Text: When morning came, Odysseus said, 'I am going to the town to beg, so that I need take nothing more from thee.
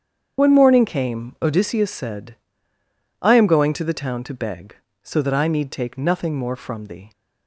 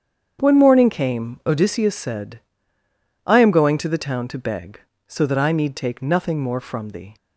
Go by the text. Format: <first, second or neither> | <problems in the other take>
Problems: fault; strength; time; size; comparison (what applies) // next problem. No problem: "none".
second | loses the start of "When"; at 0.3 s; 40 ms // starts louder than the rest; strong; until 1.4 s; 7.5 dB; strong in the second